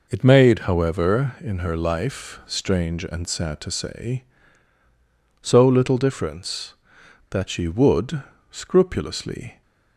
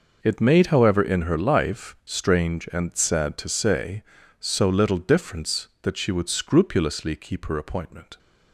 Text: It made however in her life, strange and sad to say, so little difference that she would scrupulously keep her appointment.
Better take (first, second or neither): second